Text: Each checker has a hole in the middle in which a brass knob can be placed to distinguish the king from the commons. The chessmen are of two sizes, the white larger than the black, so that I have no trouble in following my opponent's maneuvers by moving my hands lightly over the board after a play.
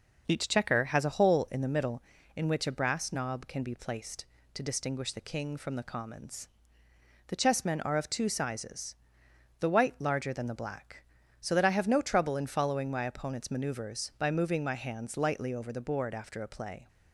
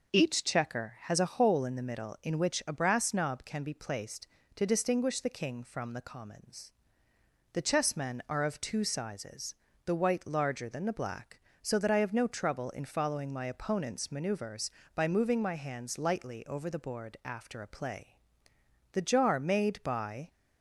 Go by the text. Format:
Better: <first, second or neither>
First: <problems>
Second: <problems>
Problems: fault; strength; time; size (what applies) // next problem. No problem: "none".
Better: first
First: none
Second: goes on to say "The jar made by"; from 18.9 s on; 1.3 s long